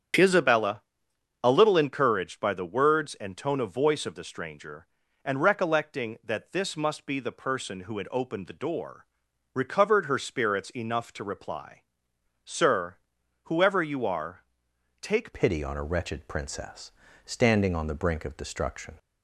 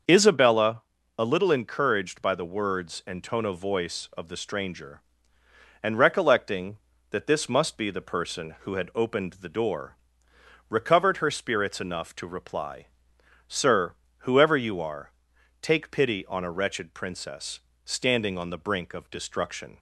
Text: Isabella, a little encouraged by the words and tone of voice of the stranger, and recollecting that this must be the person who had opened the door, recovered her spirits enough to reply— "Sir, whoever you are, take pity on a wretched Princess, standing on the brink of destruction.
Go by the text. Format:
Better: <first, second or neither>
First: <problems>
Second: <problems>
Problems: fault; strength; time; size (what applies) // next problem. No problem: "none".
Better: second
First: starts louder than the rest; strong; until 1.8 s; 8.5 dB // changes voice at "pity"; from 15.3 s on; 3.6 s long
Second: starts louder than the rest; until 1.4 s; 6.5 dB